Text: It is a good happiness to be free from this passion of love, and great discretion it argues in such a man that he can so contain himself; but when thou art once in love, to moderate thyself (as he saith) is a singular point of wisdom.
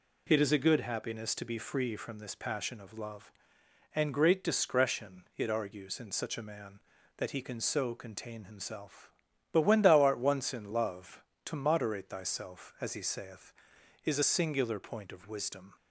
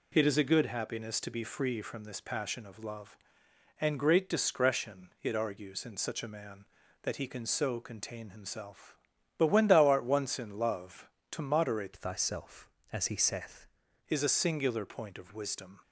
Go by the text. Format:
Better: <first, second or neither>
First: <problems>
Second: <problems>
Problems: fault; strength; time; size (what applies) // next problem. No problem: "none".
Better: first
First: none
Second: changes voice from "thyself" to "saith"; from 11.9 to 13.6 s; 1.7 s long